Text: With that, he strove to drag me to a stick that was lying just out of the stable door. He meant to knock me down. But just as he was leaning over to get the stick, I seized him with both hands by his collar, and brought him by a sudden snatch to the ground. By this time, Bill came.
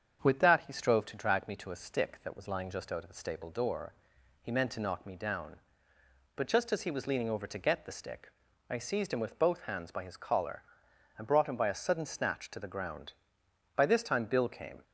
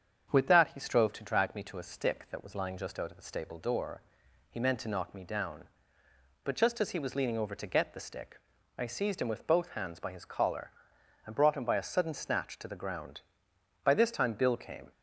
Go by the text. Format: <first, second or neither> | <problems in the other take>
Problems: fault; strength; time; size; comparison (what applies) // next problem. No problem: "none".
neither | starts louder than the rest; strong; the same in both